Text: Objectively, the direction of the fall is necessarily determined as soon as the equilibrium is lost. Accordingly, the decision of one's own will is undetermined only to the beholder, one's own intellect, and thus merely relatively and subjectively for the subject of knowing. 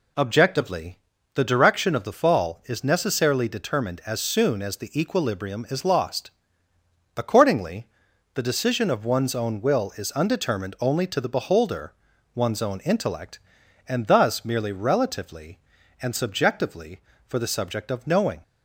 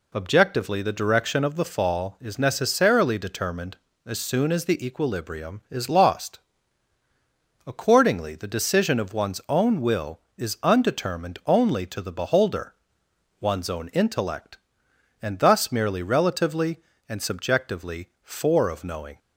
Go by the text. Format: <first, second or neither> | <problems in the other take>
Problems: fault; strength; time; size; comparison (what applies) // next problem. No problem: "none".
first | skips "the subject"; at 18.6 s